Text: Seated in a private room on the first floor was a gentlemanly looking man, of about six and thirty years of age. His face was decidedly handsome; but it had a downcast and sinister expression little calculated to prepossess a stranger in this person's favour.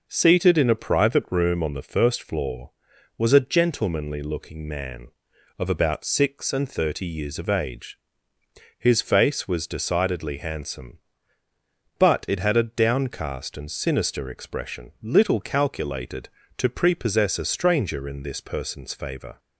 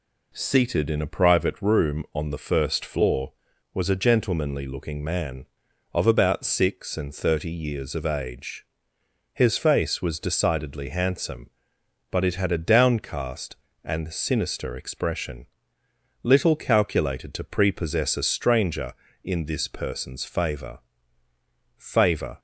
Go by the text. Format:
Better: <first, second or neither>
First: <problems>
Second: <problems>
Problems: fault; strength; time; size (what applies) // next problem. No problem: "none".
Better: first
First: none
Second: pauses between "expression" and "little"; noticeable; at 15.4 s; 0.78 s long // says "favour" twice; at 21.7 s